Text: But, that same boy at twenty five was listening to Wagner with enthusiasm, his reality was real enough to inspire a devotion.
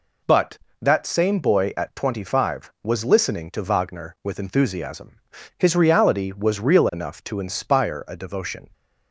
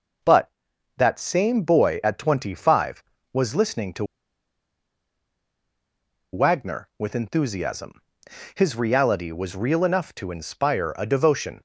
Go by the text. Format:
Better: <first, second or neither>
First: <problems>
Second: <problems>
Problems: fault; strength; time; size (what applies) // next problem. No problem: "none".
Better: first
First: none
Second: pauses between "to" and "Wagner"; strong; at 4.0 s; 2.2 s long